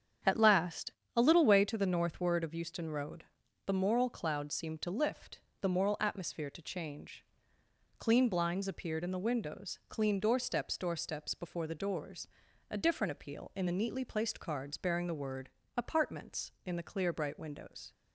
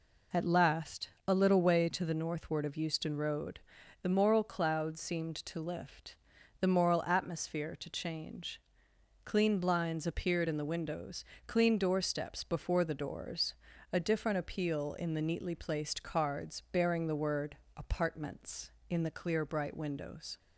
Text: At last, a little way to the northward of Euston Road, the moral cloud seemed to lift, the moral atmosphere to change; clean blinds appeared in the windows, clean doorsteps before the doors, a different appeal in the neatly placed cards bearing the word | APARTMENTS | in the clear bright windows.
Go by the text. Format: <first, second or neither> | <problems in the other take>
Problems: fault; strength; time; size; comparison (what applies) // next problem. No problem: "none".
second | starts louder than the rest; strong; until 1.4 s; 8 dB // says "doorsteps" twice; at 10.7 s